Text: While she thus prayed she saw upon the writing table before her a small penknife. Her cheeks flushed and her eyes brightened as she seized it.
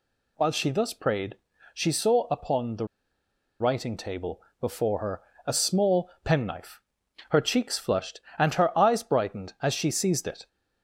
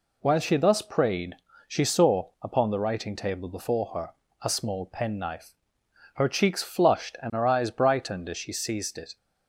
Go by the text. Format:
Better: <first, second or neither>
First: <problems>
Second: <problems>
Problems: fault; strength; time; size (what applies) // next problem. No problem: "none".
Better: second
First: pauses between "prayed" and "she"; slight; at 1.3 s; 0.36 s long // pauses between "the" and "writing"; noticeable; at 2.8 s; 0.75 s long // pauses between "table" and "before"; slight; at 4.4 s; 0.18 s long // pauses between "her" and "a"; slight; at 5.2 s; 0.24 s long // pauses between "small" and "penknife"; slight; at 6.0 s; 0.16 s long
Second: pauses between "prayed" and "she"; slight; at 1.3 s; 0.30 s long // pauses between "her" and "a"; slight; at 4.1 s; 0.32 s long